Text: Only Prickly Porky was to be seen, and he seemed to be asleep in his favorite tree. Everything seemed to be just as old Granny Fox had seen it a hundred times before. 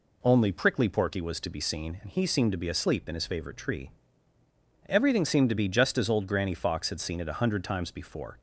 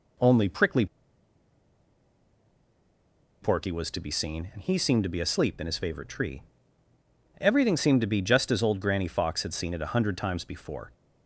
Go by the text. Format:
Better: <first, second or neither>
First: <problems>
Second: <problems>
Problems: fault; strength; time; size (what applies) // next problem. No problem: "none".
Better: first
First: none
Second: pauses between "Prickly" and "Porky"; strong; at 0.8 s; 2.5 s long